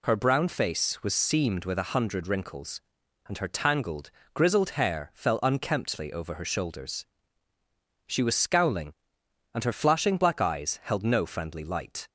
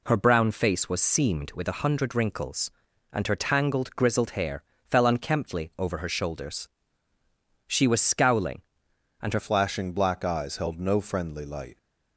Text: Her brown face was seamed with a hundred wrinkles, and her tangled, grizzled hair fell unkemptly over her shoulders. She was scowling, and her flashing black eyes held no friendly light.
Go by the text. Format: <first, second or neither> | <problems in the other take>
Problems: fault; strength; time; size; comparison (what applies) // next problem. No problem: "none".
first | pauses between "hair" and "fell"; slight; at 4.6 s; 0.26 s long // changes voice at "flashing"; from 9.3 s on; 2.4 s long